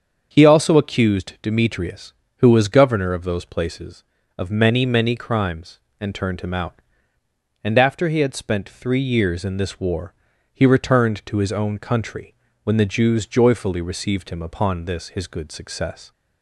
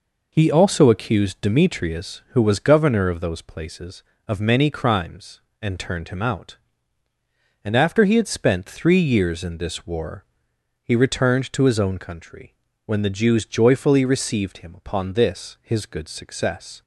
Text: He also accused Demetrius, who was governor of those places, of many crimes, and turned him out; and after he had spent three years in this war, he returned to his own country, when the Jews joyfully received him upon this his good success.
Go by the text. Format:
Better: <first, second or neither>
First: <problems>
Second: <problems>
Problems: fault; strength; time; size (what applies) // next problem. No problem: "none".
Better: second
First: starts louder than the rest; until 1.3 s; 7 dB // says "many" twice; at 4.8 s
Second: none